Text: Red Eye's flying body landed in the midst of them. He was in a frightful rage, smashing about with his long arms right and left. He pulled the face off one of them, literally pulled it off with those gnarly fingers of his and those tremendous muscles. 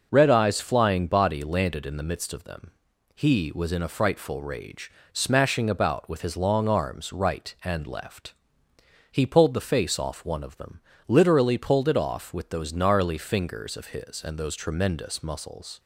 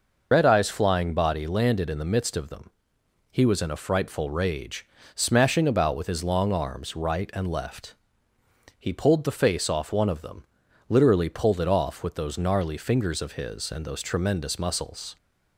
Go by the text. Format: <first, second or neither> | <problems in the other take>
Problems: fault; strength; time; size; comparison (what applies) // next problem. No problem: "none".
first | loses the start of "Red"; at 0.3 s; 70 ms